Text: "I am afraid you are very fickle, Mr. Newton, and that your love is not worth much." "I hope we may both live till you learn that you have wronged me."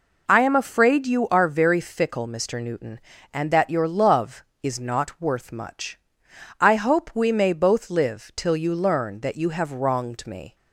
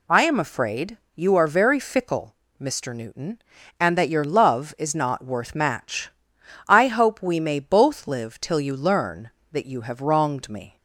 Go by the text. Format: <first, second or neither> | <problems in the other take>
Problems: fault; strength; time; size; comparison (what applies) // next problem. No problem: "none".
first | pauses between "afraid" and "you"; slight; at 0.9 s; 0.18 s long // says "match" for "much"; at 5.5 s